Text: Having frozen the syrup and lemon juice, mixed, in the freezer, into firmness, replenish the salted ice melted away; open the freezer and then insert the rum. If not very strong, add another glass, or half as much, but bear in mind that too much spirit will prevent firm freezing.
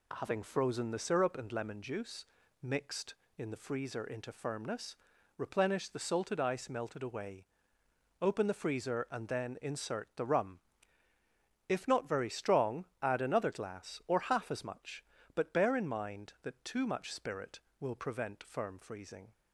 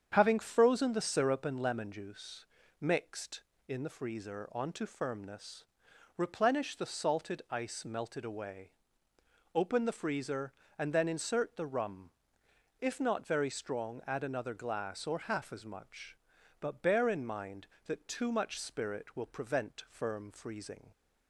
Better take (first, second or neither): first